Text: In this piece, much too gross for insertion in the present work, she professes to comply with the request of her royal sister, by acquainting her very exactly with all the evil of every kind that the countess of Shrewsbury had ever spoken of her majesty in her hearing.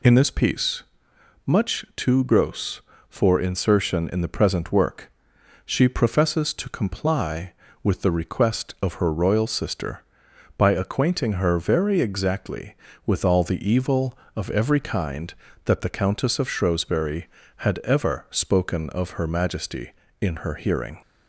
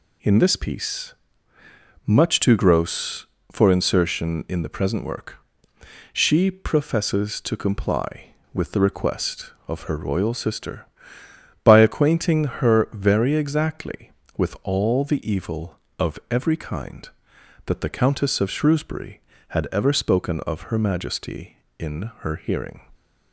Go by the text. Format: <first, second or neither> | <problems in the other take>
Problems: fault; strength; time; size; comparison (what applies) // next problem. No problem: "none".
neither | none